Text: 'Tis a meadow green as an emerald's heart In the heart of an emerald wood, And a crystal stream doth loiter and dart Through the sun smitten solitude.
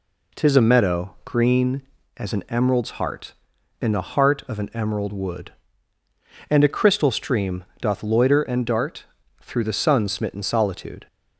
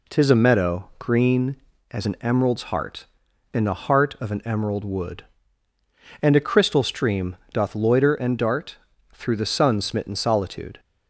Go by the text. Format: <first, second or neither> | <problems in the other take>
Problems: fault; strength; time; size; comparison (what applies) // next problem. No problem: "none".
neither | pauses between "stream" and "doth"; slight; the same in both // pauses between "dart" and "Through"; the same in both